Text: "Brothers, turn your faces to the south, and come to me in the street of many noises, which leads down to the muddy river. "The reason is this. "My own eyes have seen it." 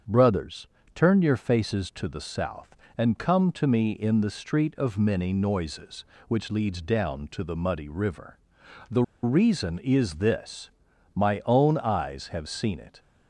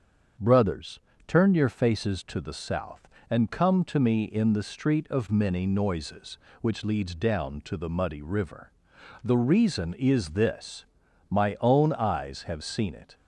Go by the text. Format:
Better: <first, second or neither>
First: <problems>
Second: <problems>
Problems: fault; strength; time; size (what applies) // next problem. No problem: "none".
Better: second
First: starts louder than the rest; strong; until 1.3 s; 7.5 dB // pauses between "The" and "reason"; slight; at 9.0 s; 0.19 s long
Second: starts louder than the rest; strong; until 1.6 s; 7 dB